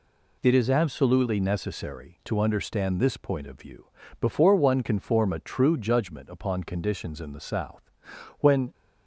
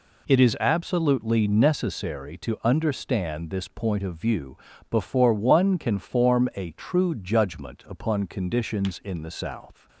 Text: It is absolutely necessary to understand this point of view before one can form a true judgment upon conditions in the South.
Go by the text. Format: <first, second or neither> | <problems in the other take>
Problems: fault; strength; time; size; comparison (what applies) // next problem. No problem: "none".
second | pauses between "view" and "before"; slight; at 3.8 s; 0.34 s long; slight in the second // goes on to say "When"; slight; from 8.4 s on; 0.32 s long